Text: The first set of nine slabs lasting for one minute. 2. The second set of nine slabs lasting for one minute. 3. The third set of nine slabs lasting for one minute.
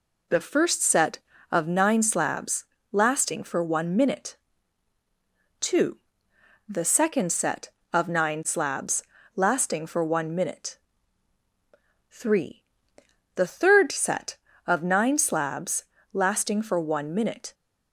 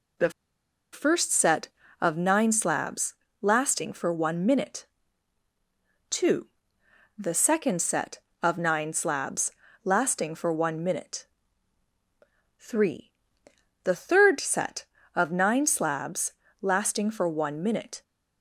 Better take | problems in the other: first | pauses between "The" and "first"; noticeable; at 0.2 s; 0.62 s long // pauses between "slabs" and "lasting"; slight; at 3.1 s; 0.26 s long; slight in the first // pauses between "slabs" and "lasting"; slight; at 9.5 s; 0.32 s long; slight in the first // pauses between "slabs" and "lasting"; slight; at 16.3 s; 0.28 s long; slight in the first

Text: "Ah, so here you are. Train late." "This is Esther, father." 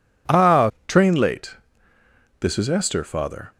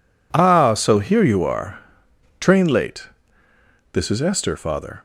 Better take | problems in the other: second | skips "so here you are"; at 0.7 s

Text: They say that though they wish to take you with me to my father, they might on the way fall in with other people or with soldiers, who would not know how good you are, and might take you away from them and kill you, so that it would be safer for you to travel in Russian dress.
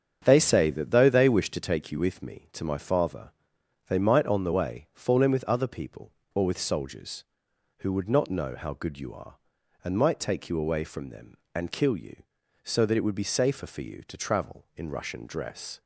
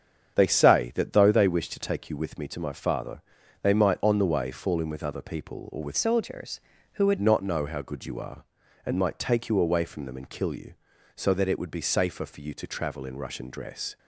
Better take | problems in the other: first | starts louder than the rest; strong; until 1.3 s; 7.5 dB; strong in the first // changes voice from "soldiers" to "would"; from 5.9 to 7.1 s; 1.2 s long

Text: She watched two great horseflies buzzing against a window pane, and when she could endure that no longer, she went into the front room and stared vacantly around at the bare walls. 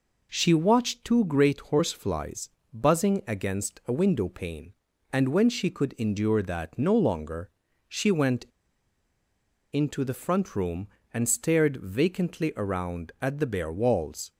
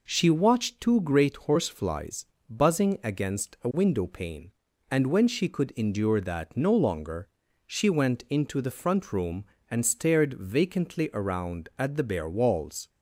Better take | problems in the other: second | pauses between "horseflies" and "buzzing"; slight; at 2.5 s; 0.22 s long; slight in the second // pauses between "went" and "into"; strong; at 8.4 s; 1.2 s long

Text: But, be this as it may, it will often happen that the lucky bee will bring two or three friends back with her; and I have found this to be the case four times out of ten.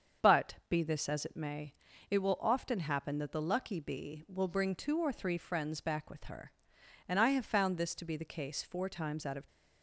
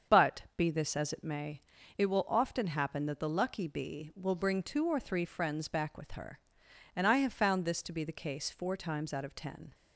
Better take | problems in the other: second | starts louder than the rest; until 1.3 s; 7 dB; also in the second // stops before "ten"; at 9.4 s

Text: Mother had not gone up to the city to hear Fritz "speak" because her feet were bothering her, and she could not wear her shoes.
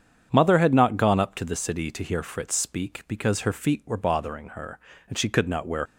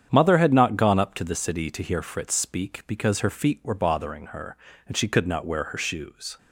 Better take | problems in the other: second | starts louder than the rest; strong; until 1.3 s; 8 dB; strong in the second // stops before "her shoes"; at 5.8 s

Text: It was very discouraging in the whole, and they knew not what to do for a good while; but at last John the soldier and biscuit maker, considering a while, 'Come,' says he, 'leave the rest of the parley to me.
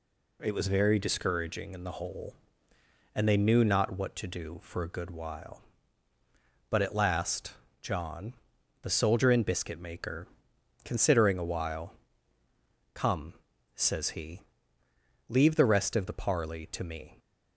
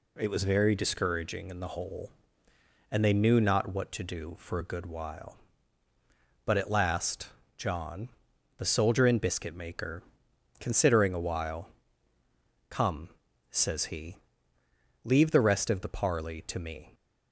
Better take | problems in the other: neither | pauses between "last" and "John"; slight; the same in both // pauses between "John" and "the"; noticeable; the same in both

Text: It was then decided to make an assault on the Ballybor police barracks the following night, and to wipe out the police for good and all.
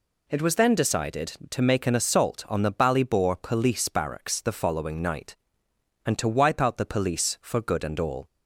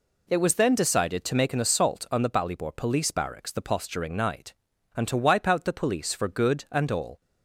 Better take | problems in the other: first | says "posturing" for "following"; at 3.6 s

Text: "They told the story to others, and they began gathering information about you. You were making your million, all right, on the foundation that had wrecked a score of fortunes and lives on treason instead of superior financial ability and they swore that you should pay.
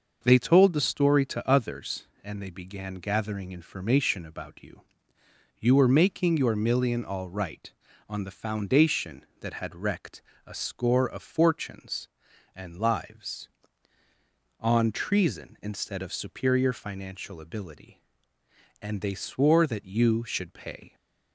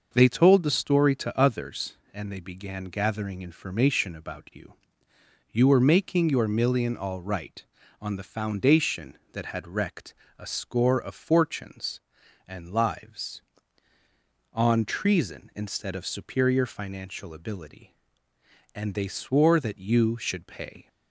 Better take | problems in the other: neither | starts louder than the rest; noticeable; the same in both // pauses between "wrecked" and "a"; slight; the same in both

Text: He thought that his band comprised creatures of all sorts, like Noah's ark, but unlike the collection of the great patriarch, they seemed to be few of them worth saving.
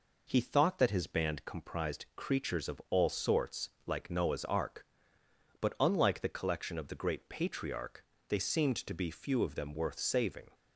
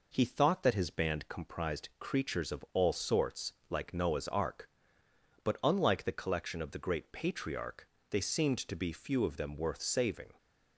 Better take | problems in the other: neither | none

